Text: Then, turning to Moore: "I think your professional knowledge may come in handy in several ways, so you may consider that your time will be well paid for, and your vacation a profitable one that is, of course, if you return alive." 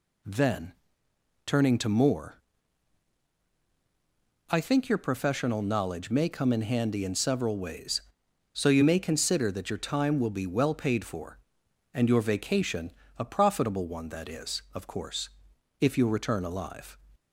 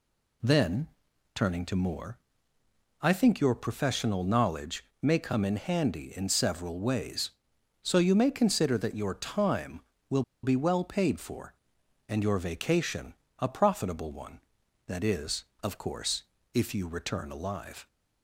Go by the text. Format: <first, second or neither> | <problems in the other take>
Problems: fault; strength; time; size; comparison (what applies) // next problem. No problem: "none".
first | pauses between "knowledge" and "may"; slight; at 4.8 s; 0.16 s long // pauses between "will" and "be"; slight; at 10.2 s; 0.21 s long // pauses between "vacation" and "a"; slight; at 13.1 s; 0.26 s long; slight in the first